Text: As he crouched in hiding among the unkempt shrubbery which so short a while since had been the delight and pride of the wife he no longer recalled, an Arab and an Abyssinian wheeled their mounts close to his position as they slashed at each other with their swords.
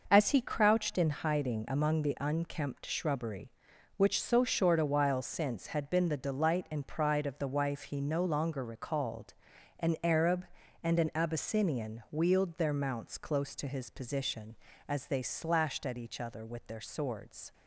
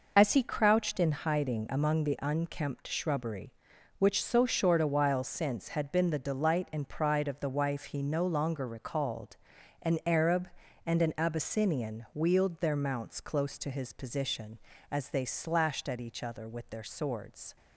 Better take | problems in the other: first | loses the start of "As"; at 0.1 s; 80 ms

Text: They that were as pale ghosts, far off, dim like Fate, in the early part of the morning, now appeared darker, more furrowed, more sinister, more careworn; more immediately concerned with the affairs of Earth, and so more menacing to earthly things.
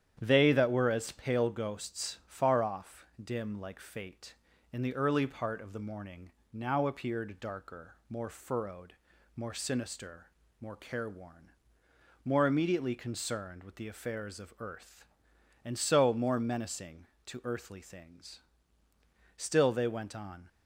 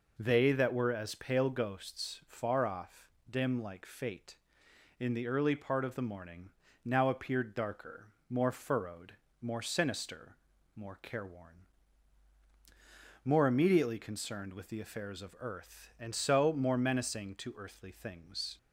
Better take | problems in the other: second | starts louder than the rest; strong; until 1.2 s; 9.5 dB // goes on to say "Still they went on"; noticeable; from 19.3 s on; 1.1 s long

